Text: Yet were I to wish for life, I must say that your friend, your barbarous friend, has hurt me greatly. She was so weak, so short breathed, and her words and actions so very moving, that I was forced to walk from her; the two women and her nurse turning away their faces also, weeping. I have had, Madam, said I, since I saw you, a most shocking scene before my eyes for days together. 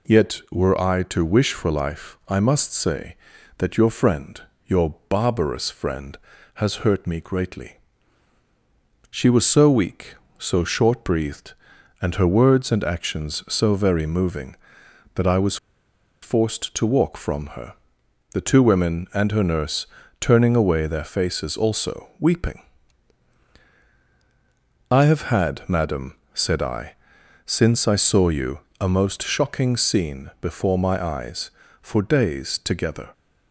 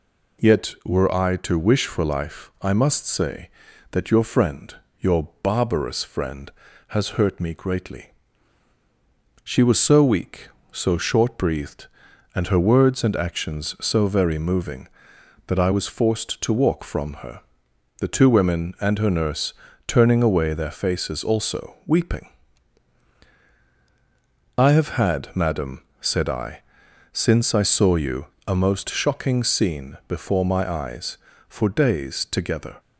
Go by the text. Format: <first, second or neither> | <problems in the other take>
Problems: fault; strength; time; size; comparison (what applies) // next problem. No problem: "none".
second | pauses between "was" and "forced"; noticeable; at 15.5 s; 0.66 s long // pauses between "nurse" and "turning"; slight; at 19.8 s; 0.32 s long; slight in the second